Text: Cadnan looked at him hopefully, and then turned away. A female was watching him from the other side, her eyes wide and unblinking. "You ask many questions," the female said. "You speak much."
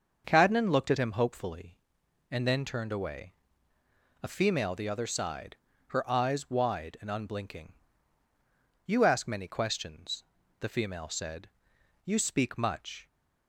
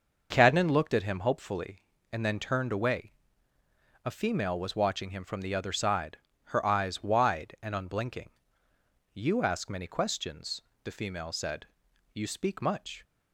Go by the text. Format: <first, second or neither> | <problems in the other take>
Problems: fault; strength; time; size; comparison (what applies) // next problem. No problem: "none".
second | starts louder than the rest; until 1.2 s; 6.5 dB; noticeable in the second // skips "was watching him from"; at 4.7 s